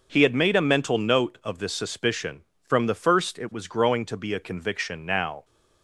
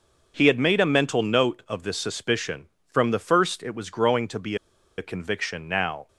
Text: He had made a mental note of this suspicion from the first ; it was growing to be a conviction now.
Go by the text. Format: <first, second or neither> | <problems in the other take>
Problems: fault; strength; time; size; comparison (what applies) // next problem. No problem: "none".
first | pauses between "be" and "a"; at 4.5 s; 0.40 s long